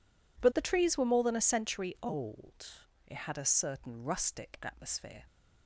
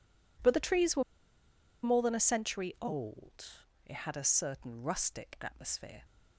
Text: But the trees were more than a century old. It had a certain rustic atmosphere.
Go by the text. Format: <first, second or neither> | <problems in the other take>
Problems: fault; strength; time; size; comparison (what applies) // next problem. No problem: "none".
first | pauses between "were" and "more"; noticeable; at 1.0 s; 0.81 s long